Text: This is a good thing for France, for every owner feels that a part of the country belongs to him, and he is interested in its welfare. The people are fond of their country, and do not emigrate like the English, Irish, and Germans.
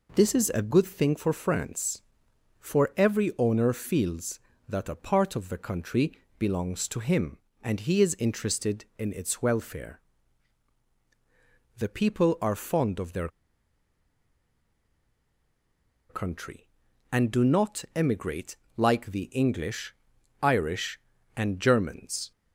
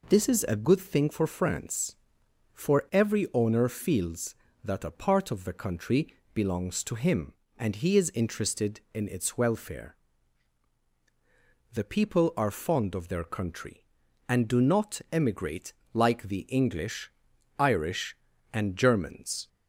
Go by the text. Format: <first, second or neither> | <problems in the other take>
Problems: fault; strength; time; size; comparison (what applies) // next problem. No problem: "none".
second | pauses between "country" and "belongs"; slight; at 6.1 s; 0.18 s long; slight in the second // pauses between "their" and "country"; strong; at 13.2 s; 2.8 s long // pauses between "emigrate" and "like"; slight; at 18.5 s; 0.20 s long; slight in the second